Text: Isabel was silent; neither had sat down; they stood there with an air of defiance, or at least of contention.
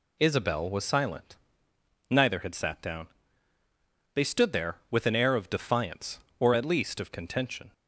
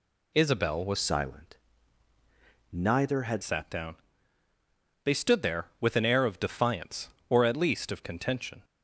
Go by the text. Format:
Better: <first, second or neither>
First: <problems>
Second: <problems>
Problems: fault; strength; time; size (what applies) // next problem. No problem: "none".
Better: first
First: none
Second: changes voice from "silent" to "had"; from 0.9 to 3.4 s; 2.5 s long